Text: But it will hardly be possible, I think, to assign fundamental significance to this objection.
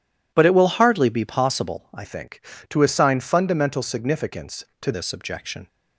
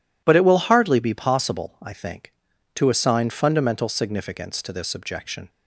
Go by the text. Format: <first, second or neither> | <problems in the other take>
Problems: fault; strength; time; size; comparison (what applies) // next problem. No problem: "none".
second | changes voice from "think" to "to"; from 2.0 to 4.9 s; 2.9 s long